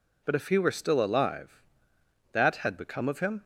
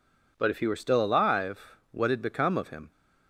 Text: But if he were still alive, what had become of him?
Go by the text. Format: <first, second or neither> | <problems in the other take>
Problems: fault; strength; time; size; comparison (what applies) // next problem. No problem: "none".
second | says "that" for "what"; at 2.3 s